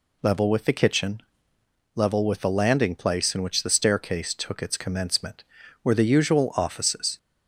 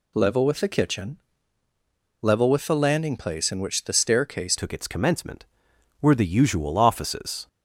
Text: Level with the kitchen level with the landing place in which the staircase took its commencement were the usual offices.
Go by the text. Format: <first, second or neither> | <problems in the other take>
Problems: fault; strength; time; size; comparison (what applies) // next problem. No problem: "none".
first | pauses between "kitchen" and "level"; at 1.1 s; 1.0 s long; noticeable in the first // changes voice at "took"; from 4.5 s on; 2.9 s long